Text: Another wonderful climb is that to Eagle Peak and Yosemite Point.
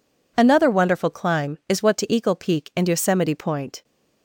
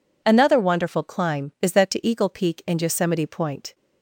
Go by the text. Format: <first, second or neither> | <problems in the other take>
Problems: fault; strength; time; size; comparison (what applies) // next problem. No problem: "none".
second | says "what" for "that"; at 1.8 s